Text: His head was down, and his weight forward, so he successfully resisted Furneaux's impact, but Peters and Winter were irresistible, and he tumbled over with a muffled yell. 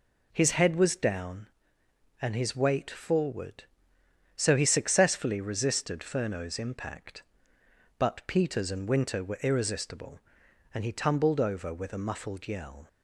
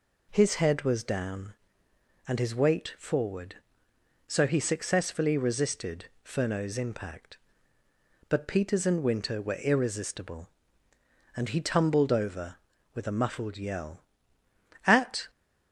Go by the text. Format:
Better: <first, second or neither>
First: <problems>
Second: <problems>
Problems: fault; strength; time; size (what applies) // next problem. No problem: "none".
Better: first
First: none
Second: pauses between "resisted" and "Furneaux's"; slight; at 6.0 s; 0.16 s long // goes on to say "At"; slight; from 14.8 s on; 0.44 s long